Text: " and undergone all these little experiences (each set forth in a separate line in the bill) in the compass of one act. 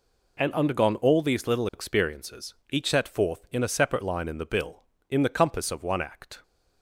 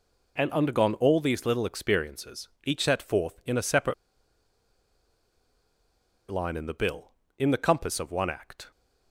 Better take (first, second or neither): first